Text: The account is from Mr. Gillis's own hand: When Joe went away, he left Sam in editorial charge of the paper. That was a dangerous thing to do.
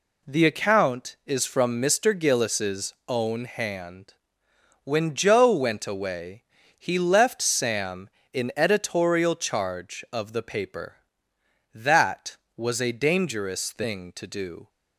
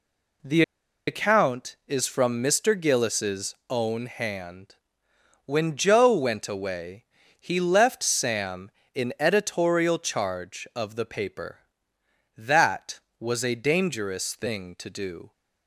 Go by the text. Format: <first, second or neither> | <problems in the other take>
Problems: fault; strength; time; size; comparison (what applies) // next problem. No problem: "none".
first | pauses between "The" and "account"; at 0.6 s; 0.45 s long